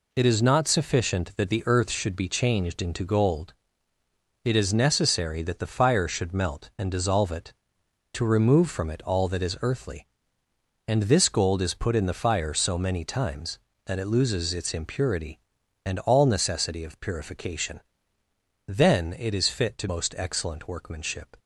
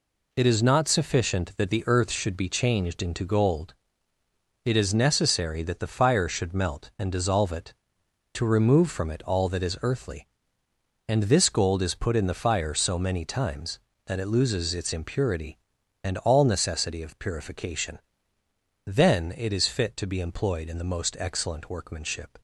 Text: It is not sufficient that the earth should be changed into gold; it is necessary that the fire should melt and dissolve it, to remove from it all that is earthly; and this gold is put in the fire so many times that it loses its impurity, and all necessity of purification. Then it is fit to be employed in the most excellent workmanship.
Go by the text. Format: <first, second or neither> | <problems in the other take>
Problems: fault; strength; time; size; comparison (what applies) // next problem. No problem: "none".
second | skips "be employed in the"; at 19.8 s